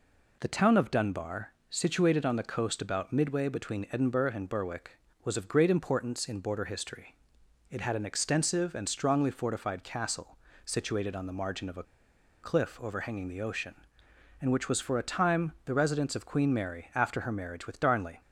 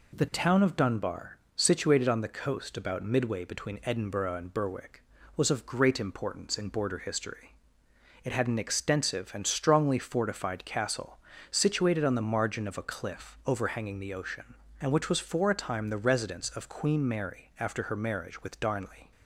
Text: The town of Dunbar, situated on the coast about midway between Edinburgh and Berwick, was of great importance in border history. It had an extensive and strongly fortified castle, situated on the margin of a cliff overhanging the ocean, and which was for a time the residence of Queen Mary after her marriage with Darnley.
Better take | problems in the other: second | pauses between "a" and "cliff"; noticeable; at 11.8 s; 0.59 s long

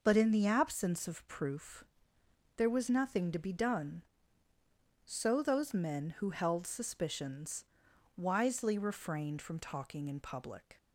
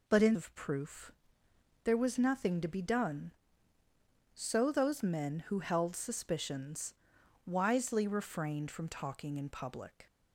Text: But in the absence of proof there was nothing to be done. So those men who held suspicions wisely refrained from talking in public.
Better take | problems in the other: first | skips "the absence"; at 0.3 s // pauses between "proof" and "there"; noticeable; at 1.1 s; 0.72 s long; noticeable in the first // pauses between "suspicions" and "wisely"; noticeable; at 6.9 s; 0.52 s long; noticeable in the first

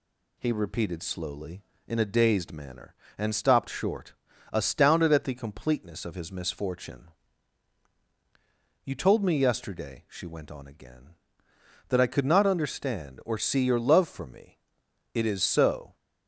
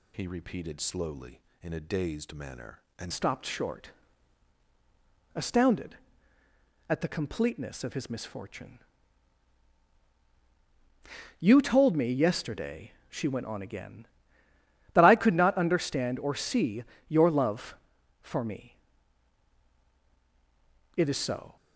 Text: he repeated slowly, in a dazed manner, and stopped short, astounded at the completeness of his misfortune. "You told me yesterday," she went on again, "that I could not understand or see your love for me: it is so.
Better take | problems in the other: first | changes voice at "stopped"; from 3.1 s on; 18.4 s long // pauses between "see" and "your"; slight; at 16.8 s; 0.24 s long

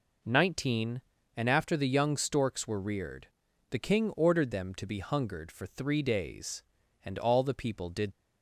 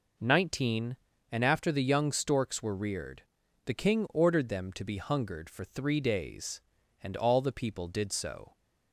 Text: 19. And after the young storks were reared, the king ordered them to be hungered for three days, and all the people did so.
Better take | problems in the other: second | stops before "so"; at 8.1 s

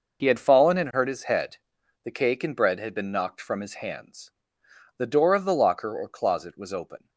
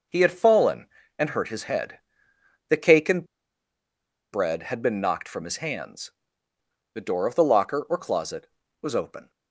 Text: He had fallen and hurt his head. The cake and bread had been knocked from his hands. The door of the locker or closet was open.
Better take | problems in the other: first | pauses between "and" and "bread"; at 3.2 s; 1.0 s long

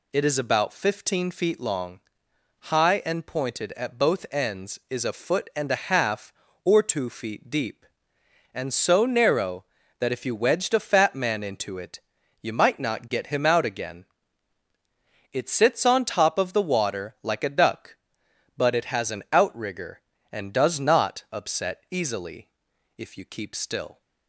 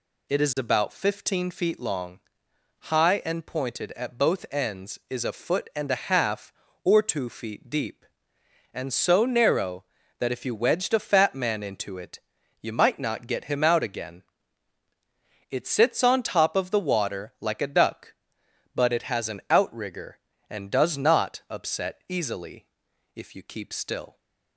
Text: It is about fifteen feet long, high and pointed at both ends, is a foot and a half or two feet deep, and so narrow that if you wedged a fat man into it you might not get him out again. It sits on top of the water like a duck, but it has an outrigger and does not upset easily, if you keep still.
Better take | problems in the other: neither | pauses between "it" and "you"; the same in both

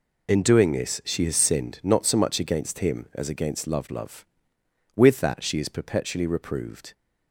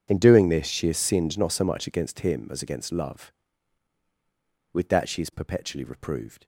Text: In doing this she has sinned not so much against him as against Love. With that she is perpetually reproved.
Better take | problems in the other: second | says "Love" twice; at 3.9 s

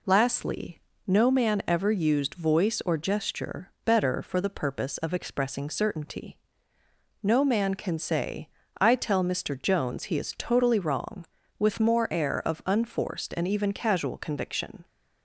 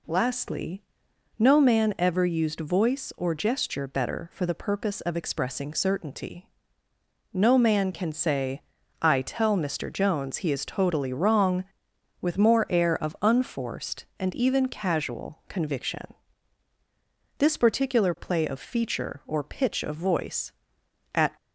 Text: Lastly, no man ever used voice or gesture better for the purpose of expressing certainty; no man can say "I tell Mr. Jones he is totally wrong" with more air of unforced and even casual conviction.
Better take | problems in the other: first | pauses between "say" and "I"; at 8.6 s; 0.38 s long; slight in the first // goes on to say "This particular play of feature or pitch of voice at"; strong; from 17.3 s on; 3.9 s long

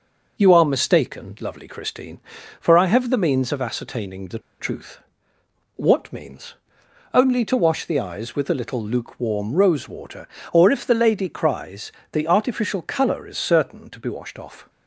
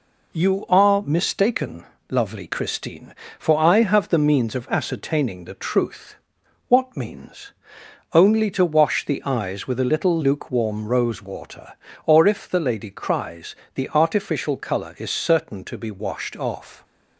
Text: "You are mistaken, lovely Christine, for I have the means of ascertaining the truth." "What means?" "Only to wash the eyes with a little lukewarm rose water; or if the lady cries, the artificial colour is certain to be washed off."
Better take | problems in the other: second | pauses between "the" and "truth"; slight; at 4.3 s; 0.21 s long

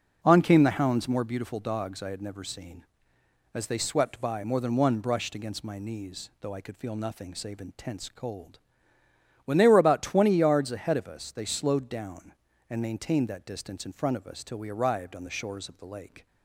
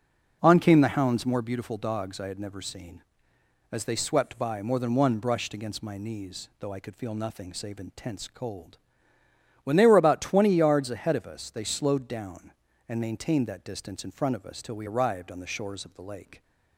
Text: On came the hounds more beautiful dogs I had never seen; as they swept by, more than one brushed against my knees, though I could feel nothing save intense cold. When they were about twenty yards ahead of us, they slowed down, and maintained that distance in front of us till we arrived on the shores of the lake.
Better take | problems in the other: neither | none

